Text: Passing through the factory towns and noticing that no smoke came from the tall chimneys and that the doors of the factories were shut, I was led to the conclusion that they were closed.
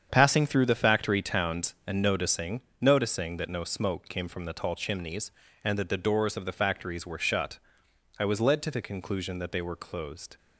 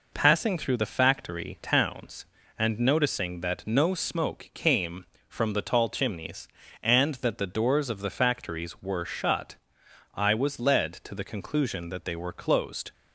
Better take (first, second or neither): second